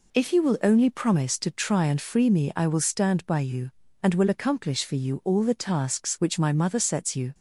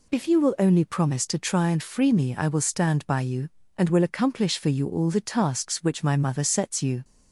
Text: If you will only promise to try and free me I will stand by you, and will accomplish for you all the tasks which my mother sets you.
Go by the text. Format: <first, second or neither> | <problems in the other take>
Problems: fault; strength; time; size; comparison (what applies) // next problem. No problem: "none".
neither | none